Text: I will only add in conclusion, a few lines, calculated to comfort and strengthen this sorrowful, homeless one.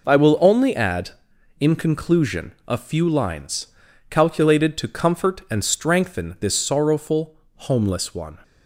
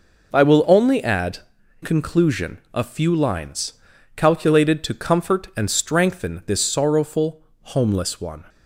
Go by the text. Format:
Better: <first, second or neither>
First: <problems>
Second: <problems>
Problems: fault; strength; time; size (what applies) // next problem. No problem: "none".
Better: first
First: none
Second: skips "in"; at 1.6 s